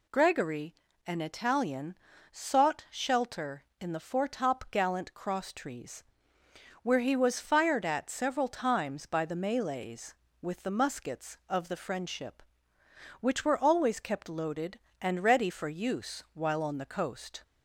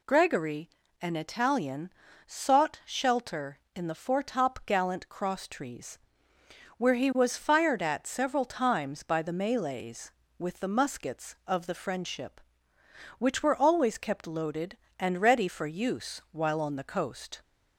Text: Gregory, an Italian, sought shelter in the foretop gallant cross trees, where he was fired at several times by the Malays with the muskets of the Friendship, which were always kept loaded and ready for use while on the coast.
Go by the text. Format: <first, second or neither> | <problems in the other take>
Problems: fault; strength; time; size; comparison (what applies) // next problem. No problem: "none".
neither | none